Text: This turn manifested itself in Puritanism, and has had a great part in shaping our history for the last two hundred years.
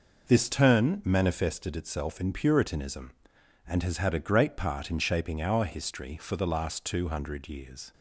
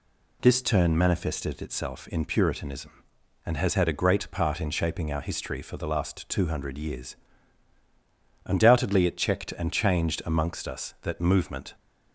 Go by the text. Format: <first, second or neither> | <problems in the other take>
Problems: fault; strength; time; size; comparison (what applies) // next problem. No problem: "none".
first | goes on to say "Undoubtedly it checked and changed amongst us that movement"; strong; from 8.4 s on; 3.2 s long